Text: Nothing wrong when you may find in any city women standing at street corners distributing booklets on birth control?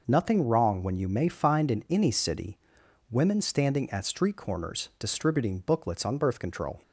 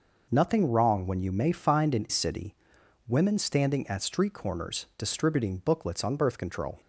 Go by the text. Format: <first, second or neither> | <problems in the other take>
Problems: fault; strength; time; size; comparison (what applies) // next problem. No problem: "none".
first | skips "any"; at 2.0 s // pauses between "city" and "women"; noticeable; at 2.5 s; 0.52 s long; noticeable in the first